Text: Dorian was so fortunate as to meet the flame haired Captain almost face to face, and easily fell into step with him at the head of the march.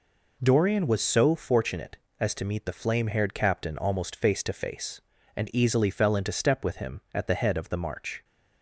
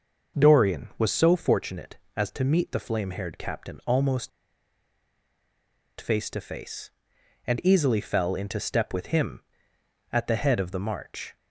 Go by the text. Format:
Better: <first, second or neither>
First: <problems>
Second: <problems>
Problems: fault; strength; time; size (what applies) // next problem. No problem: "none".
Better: first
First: none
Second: pauses between "almost" and "face"; strong; at 4.2 s; 1.7 s long